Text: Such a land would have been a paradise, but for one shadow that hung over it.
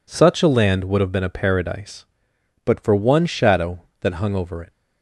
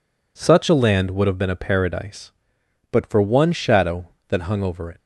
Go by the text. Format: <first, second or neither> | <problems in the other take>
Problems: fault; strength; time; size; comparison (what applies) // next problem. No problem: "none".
neither | none